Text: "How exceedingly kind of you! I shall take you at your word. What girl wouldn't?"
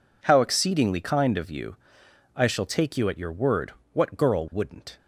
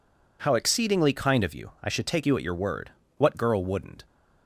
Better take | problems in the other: first | says "should" for "shall"; at 1.9 s

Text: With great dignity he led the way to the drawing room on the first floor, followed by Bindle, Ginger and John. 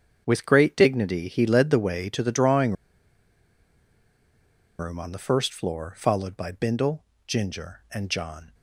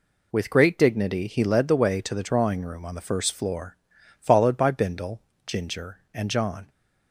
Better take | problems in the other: second | starts louder than the rest; strong; until 1.2 s; 7.5 dB // pauses between "drawing" and "room"; strong; at 2.7 s; 2.0 s long

